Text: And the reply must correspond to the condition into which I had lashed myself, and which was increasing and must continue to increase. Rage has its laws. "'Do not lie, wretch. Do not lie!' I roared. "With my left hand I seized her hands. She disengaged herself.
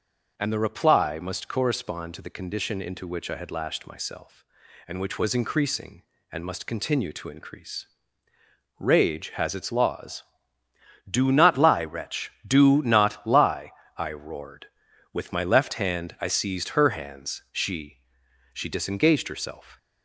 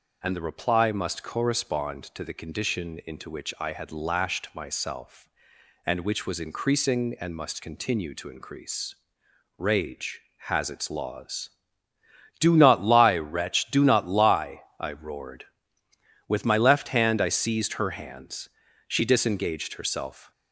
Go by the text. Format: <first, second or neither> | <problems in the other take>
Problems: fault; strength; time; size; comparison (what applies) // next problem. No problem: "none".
second | says "She" twice; at 18.5 s